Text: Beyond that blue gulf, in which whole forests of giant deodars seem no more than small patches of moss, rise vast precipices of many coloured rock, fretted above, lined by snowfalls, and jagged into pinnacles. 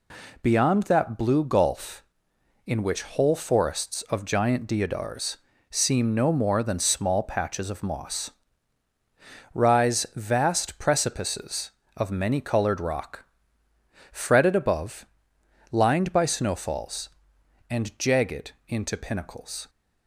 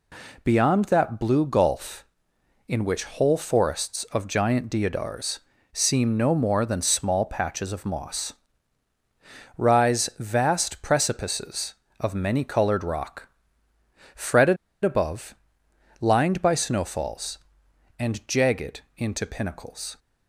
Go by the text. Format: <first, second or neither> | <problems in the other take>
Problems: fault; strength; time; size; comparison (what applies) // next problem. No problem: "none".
first | pauses between "deodars" and "seem"; slight; at 5.3 s; 0.34 s long; slight in the first // pauses between "fretted" and "above"; slight; at 14.5 s; 0.28 s long // pauses between "jagged" and "into"; slight; at 18.8 s; 0.16 s long; slight in the first